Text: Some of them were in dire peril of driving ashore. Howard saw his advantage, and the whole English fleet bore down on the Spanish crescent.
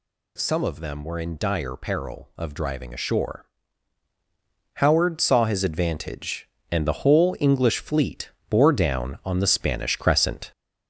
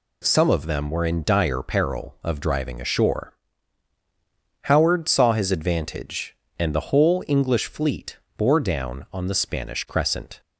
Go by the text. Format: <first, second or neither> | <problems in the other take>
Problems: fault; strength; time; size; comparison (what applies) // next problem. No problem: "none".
second | gets louder; throughout; 4 dB // pauses between "fleet" and "bore"; slight; at 8.3 s; 0.18 s long; slight in the second